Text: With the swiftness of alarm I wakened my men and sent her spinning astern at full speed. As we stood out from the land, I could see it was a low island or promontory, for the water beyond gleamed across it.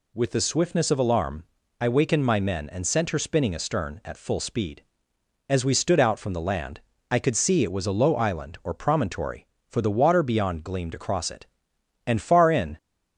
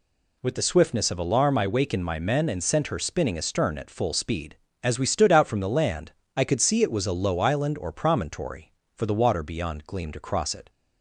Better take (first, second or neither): second